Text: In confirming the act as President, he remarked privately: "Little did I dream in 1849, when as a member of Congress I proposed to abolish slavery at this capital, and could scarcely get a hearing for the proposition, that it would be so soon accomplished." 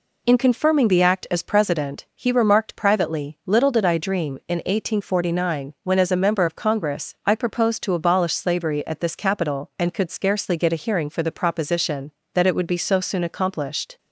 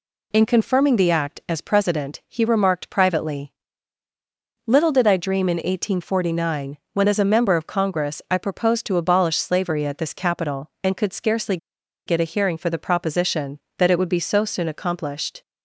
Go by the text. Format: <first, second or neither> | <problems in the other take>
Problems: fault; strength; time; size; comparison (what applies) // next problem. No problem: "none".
first | pauses between "scarcely" and "get"; noticeable; at 11.5 s; 0.49 s long